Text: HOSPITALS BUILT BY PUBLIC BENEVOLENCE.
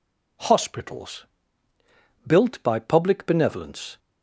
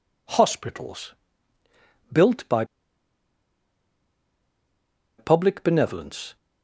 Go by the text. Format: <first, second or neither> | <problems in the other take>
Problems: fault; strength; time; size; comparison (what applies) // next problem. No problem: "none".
first | pauses between "HOSPITALS" and "BUILT"; noticeable; at 1.1 s; 0.98 s long; also in the first // pauses between "BY" and "PUBLIC"; strong; at 2.6 s; 2.5 s long